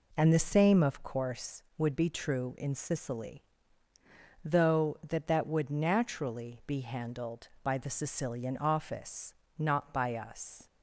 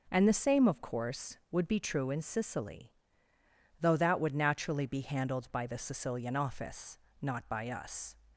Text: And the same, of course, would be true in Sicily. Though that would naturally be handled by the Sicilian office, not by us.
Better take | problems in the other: second | says "that" twice; at 5.2 s

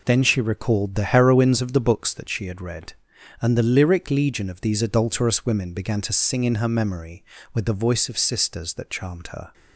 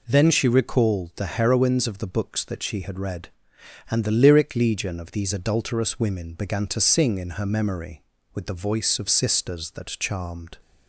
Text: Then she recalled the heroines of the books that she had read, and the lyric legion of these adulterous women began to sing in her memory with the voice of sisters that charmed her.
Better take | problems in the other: first | stops before "her"; at 10.6 s

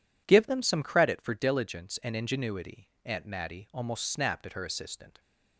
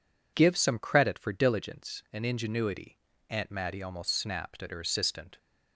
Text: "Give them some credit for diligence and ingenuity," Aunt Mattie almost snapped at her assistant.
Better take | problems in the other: first | skips "them"; at 0.5 s

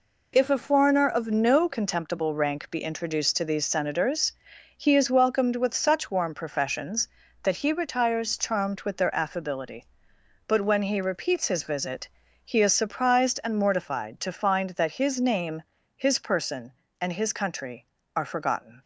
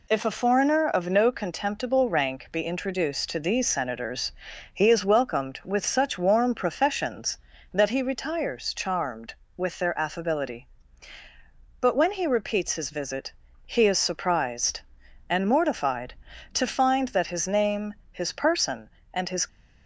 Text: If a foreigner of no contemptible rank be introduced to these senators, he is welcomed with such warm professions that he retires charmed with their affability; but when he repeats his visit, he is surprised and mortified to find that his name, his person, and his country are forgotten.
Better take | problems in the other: first | stops before "country are forgotten"; at 19.4 s

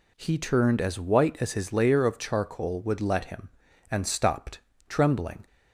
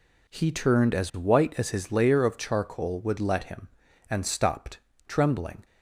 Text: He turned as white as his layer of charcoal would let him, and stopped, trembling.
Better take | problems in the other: first | gets quieter; strong; throughout; 8.5 dB

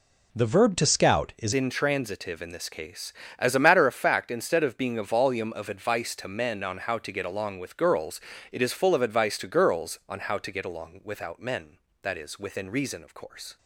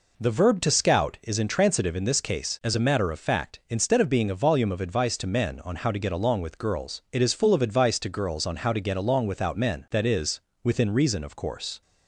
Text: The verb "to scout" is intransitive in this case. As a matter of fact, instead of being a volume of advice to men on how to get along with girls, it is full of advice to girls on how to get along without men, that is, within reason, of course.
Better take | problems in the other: second | changes voice at "intransitive"; from 1.5 s on; 12.0 s long

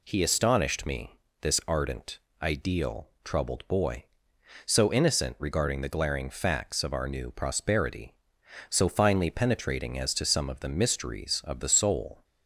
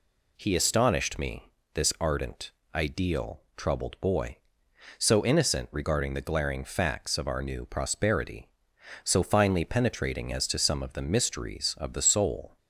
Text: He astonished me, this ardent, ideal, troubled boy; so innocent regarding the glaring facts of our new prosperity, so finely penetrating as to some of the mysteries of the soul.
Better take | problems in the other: neither | none

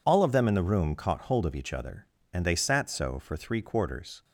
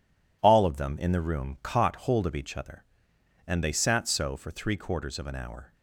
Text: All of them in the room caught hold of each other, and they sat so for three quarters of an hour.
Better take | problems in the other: second | stops before "of an hour"; at 4.2 s

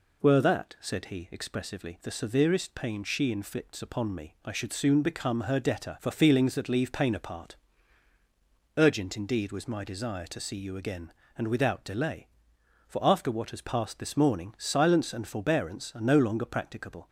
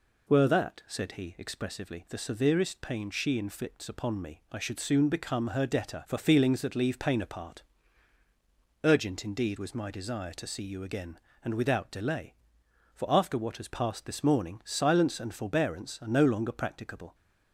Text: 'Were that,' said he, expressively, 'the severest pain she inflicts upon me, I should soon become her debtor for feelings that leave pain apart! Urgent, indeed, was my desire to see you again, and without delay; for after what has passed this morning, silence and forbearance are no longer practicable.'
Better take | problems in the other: neither | none

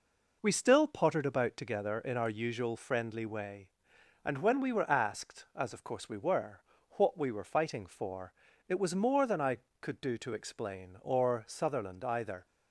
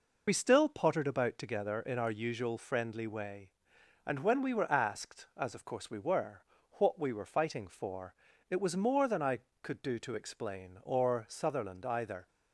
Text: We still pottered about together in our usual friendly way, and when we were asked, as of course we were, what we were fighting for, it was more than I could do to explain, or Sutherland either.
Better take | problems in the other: first | loses the start of "We"; at 0.2 s; 50 ms

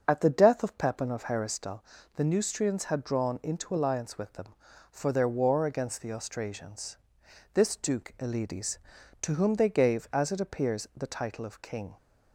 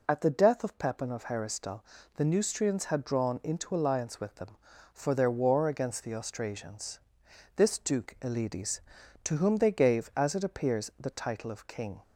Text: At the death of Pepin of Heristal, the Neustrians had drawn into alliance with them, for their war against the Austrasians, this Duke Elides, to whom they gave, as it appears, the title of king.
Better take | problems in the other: second | starts louder than the rest; until 1.7 s; 6.5 dB

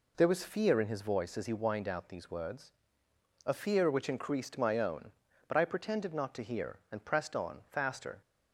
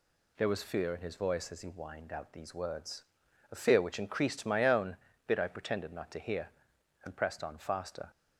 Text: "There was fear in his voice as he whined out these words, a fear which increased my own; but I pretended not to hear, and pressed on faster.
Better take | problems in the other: first | says "bit" for "but"; at 5.2 s

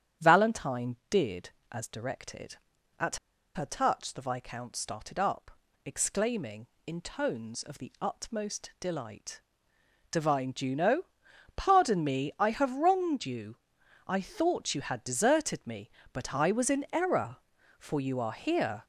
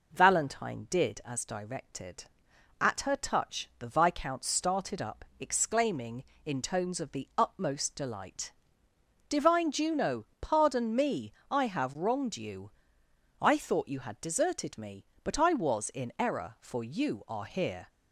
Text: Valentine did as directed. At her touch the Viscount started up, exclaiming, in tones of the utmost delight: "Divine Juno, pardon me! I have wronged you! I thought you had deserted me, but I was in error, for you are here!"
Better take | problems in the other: second | starts louder than the rest; strong; until 1.3 s; 10 dB // pauses between "At" and "her"; at 3.1 s; 0.38 s long

